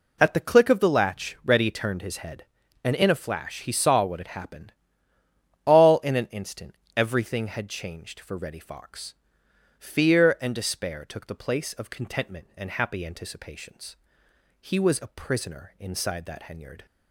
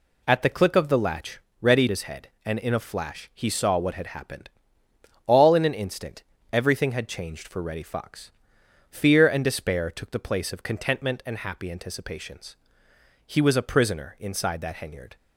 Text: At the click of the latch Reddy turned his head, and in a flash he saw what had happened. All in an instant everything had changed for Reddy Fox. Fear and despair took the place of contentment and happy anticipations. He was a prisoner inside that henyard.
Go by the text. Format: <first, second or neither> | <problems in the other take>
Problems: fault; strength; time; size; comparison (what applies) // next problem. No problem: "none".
first | pauses between "latch" and "Reddy"; slight; at 1.3 s; 0.22 s long // skips "turned"; at 1.8 s // pauses between "instant" and "everything"; slight; at 6.2 s; 0.28 s long; slight in the first